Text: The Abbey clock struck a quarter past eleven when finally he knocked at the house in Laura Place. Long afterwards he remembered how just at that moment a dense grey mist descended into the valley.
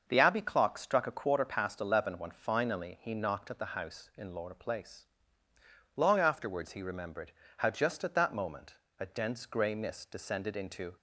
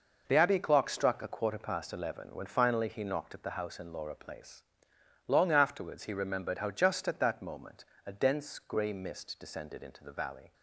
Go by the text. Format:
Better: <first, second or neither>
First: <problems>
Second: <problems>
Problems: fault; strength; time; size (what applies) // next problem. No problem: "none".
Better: second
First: starts louder than the rest; until 1.0 s; 6.5 dB // pauses between "remembered" and "how"; slight; at 7.3 s; 0.26 s long // pauses between "moment" and "a"; slight; at 8.7 s; 0.24 s long // stops before "the valley"; at 10.9 s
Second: pauses between "moment" and "a"; slight; at 7.8 s; 0.22 s long